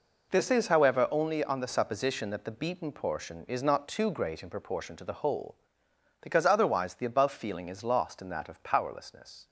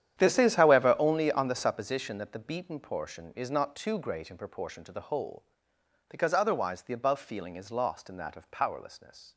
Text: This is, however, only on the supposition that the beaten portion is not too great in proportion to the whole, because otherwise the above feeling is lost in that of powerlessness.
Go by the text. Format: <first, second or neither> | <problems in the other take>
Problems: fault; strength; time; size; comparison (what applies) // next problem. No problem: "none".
first | starts louder than the rest; strong; until 1.8 s; 10 dB